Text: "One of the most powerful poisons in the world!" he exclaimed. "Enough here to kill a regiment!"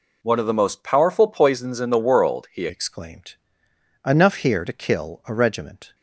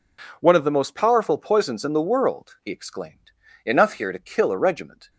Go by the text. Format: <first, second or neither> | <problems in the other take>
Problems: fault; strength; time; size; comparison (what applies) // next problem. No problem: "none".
second | changes voice at "exclaimed"; from 2.6 s on; 3.3 s long